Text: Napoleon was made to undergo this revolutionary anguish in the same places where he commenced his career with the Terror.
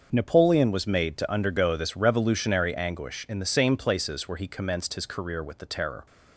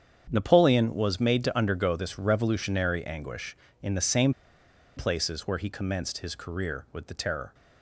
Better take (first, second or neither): first